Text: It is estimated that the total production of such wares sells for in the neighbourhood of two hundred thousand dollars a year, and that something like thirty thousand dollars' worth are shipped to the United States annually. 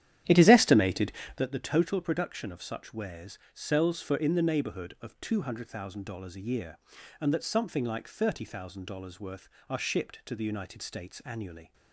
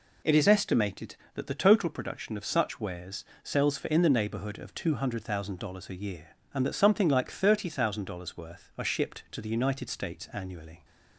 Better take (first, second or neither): second